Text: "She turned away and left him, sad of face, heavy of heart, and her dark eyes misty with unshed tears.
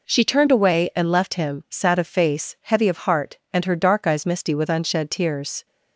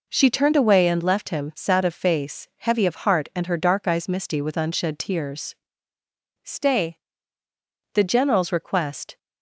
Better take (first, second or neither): first